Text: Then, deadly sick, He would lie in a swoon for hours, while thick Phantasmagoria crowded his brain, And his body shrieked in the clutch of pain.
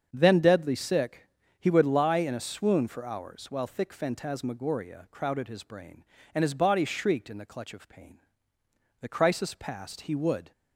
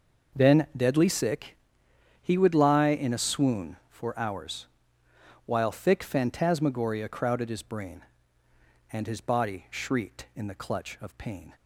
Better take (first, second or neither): second